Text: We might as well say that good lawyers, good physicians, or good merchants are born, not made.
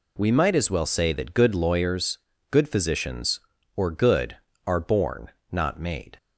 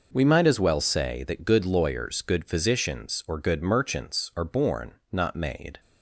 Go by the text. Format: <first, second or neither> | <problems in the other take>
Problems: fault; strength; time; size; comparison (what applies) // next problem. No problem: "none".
second | skips "merchants"; at 4.5 s